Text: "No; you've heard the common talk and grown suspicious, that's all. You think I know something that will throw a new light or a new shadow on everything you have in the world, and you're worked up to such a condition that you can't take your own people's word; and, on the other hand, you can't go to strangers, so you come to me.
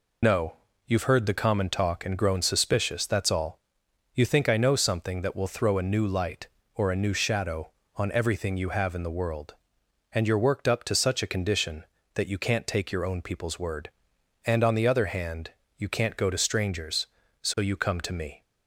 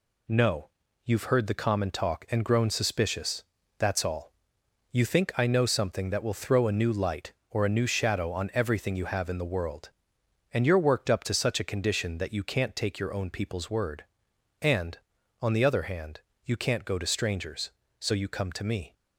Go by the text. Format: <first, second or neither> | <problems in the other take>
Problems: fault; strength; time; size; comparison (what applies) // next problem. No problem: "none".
second | loses the start of "No"; at 0.2 s; 40 ms